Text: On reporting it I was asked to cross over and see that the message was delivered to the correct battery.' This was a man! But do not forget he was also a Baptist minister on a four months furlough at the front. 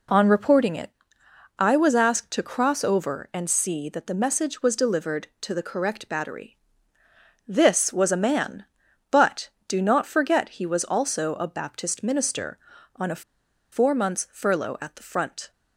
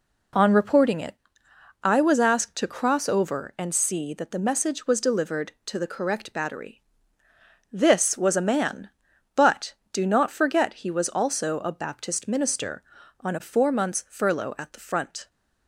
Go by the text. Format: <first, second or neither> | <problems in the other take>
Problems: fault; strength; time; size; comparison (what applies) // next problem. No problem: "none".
second | pauses between "it" and "I"; noticeable; at 0.8 s; 0.70 s long; noticeable in the second // pauses between "a" and "four"; noticeable; at 13.2 s; 0.50 s long